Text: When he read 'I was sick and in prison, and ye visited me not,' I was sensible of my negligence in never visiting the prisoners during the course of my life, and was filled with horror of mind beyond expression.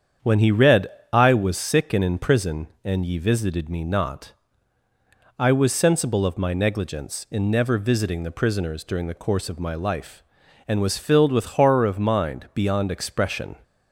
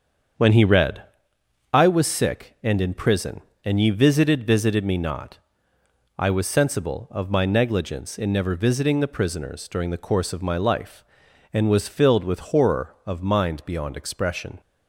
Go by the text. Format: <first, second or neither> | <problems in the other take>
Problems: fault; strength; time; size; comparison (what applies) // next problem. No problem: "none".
first | starts louder than the rest; strong; until 2.0 s; 7.5 dB; strong in the first // pauses between "read" and "I"; noticeable; at 1.0 s; 0.70 s long; slight in the first // says "visited" twice; at 4.4 s